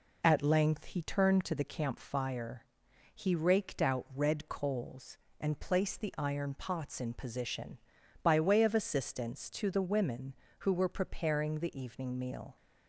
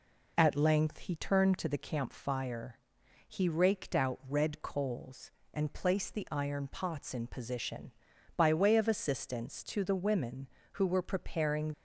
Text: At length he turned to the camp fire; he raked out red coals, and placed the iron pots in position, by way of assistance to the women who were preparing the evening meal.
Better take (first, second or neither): first